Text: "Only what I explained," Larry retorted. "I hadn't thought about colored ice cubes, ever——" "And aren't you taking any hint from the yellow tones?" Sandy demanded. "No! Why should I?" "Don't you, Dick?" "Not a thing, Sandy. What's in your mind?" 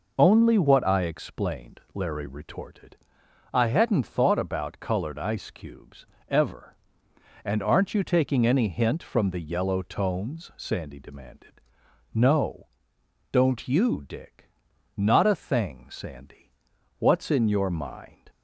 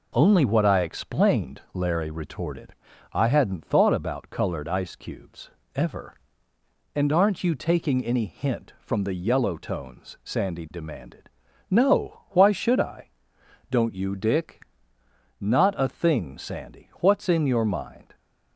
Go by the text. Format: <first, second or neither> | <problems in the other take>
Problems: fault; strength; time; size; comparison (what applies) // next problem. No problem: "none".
second | skips "Why should I"; at 12.9 s